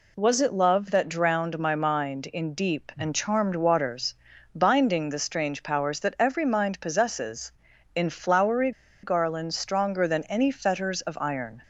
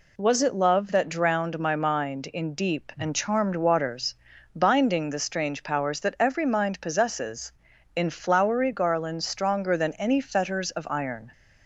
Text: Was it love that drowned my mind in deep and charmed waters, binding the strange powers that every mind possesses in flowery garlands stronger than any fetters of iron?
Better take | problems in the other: second | pauses between "flowery" and "garlands"; slight; at 8.7 s; 0.33 s long

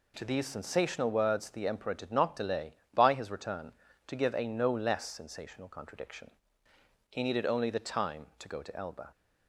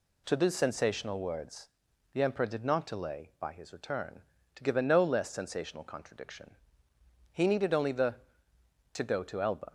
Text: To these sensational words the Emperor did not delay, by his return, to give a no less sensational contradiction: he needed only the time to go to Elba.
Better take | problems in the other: first | pauses between "words" and "the"; at 1.6 s; 0.44 s long // skips "time"; at 8.5 s

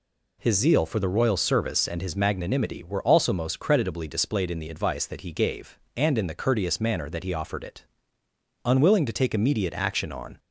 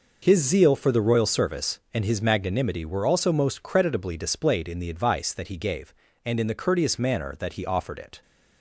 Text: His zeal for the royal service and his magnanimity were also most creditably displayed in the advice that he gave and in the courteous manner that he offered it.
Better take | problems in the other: second | goes on to say "Unwilling to take immediate action on"; strong; from 8.6 s on; 1.7 s long

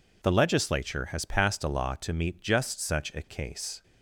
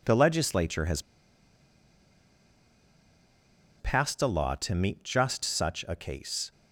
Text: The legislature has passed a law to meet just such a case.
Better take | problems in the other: first | pauses between "has" and "passed"; strong; at 0.9 s; 2.7 s long

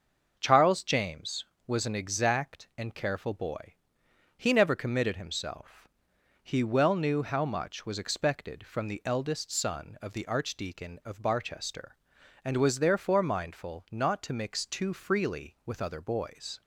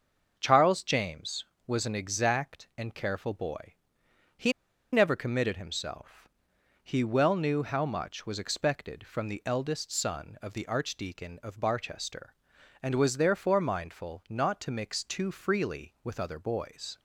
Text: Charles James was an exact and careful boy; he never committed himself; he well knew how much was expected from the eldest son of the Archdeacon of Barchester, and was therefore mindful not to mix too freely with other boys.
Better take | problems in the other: first | starts louder than the rest; until 1.3 s; 6.5 dB; also in the first // pauses between "he" and "never"; at 4.5 s; 0.41 s long

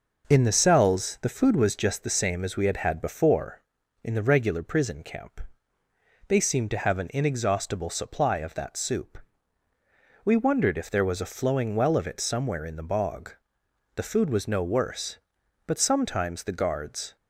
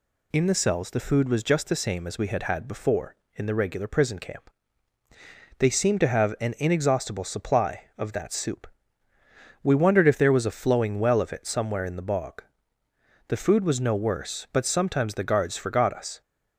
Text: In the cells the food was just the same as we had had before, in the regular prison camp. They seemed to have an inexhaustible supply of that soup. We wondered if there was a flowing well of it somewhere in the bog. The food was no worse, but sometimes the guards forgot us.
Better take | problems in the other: second | stops before "forgot us"; at 17.1 s

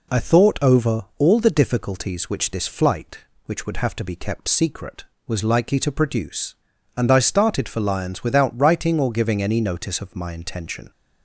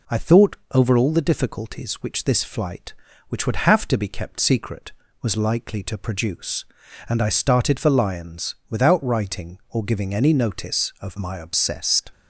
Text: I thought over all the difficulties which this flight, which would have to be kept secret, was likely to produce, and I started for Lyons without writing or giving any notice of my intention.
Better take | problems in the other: first | pauses between "thought" and "over"; slight; at 0.5 s; 0.16 s long // says "obsessed" for "intention"; at 11.3 s

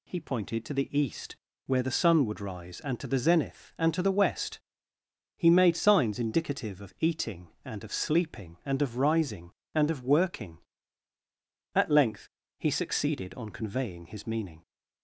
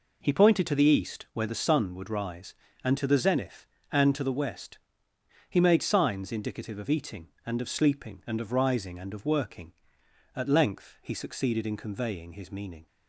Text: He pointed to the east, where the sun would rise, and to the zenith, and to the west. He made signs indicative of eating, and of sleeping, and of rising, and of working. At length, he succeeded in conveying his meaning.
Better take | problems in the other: second | says "on" for "in"; at 13.3 s

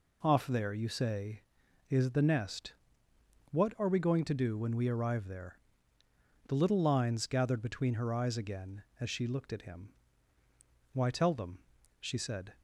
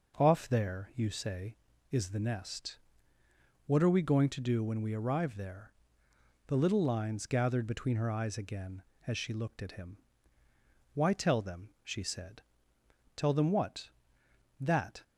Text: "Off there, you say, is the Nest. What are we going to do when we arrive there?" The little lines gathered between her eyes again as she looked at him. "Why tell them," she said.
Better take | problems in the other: first | goes on to say "Tell them what That"; strong; from 13.1 s on; 1.8 s long

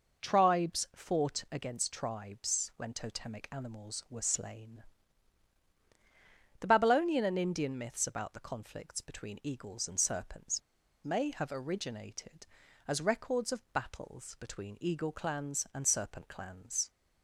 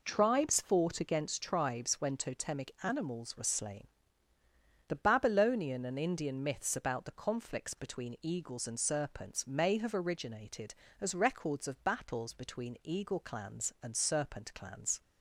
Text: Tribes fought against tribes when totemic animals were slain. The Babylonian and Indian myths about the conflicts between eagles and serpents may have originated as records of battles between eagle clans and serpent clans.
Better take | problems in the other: second | pauses between "serpents" and "may"; at 10.5 s; 0.44 s long

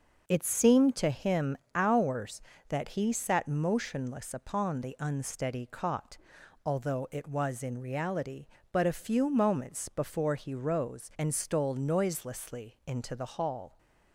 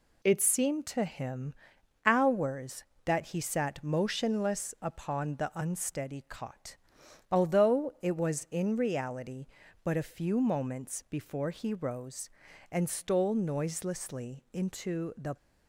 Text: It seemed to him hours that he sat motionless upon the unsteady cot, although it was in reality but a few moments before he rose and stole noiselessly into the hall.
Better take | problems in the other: first | pauses between "him" and "hours"; noticeable; at 1.5 s; 0.52 s long; slight in the first // stops before "hall"; at 15.3 s

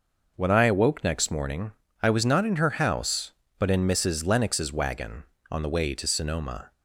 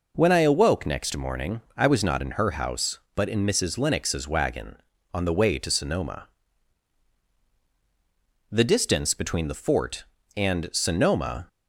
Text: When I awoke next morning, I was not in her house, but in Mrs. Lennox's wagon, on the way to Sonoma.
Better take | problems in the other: first | goes on to say "The distance between the Fort and Sonoma"; strong; from 8.4 s on; 2.9 s long

